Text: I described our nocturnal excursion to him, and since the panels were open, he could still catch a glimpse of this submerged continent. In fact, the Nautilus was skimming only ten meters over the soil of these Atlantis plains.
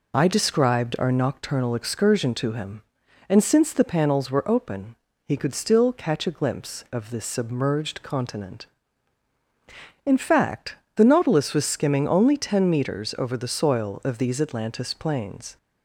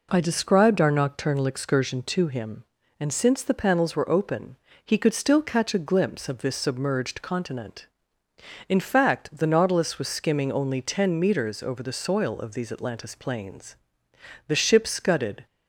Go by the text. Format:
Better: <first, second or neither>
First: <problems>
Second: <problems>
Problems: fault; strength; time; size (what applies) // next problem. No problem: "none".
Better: first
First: none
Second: goes on to say "The ship scudded"; noticeable; from 14.4 s on; 0.98 s long